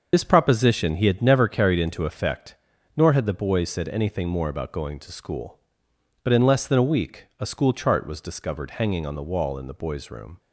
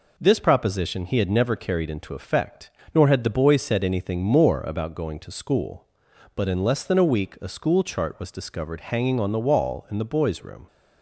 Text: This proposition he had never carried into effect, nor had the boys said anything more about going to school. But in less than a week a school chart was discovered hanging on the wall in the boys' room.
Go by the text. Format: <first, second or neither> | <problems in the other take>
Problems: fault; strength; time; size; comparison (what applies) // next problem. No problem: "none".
second | loses the start of "This"; at 0.1 s; 55 ms // starts louder than the rest; until 1.1 s; 6.5 dB // pauses between "week" and "a"; slight; at 7.2 s; 0.16 s long